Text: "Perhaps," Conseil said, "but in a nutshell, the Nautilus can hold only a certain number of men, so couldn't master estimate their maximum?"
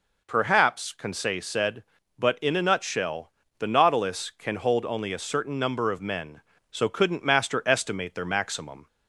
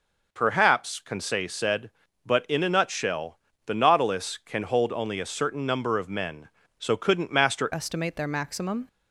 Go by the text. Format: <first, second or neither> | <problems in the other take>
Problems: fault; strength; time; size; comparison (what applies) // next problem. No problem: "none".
first | changes voice at "estimate"; from 7.7 s on; 1.1 s long